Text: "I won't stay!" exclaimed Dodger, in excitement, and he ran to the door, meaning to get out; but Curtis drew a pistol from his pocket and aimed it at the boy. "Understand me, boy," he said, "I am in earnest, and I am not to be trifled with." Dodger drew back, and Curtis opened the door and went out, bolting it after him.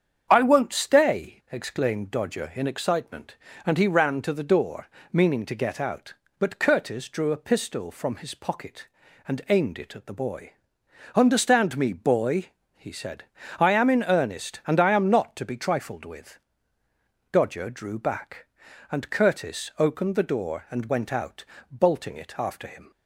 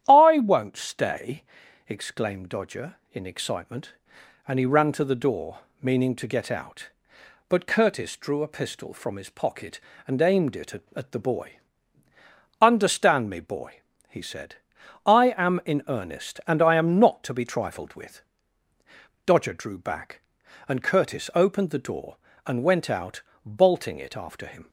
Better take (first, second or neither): first